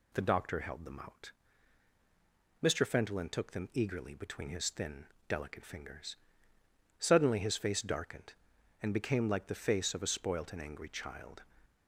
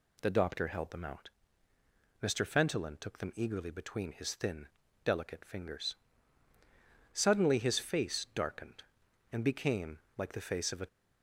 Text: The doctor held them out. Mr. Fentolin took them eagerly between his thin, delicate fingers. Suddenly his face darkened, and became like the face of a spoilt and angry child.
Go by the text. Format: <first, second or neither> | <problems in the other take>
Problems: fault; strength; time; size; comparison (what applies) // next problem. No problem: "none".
first | pauses between "became" and "like"; slight; at 9.9 s; 0.18 s long // stops before "spoilt and angry child"; at 10.8 s